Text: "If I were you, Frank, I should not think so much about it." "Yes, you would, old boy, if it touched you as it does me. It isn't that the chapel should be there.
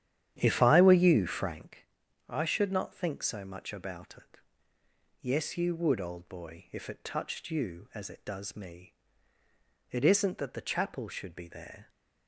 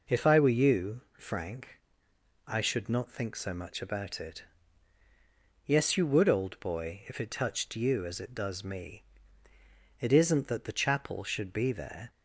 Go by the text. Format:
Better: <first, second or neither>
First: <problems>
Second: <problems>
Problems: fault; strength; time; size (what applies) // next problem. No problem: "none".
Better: second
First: starts louder than the rest; strong; until 1.6 s; 10.5 dB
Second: none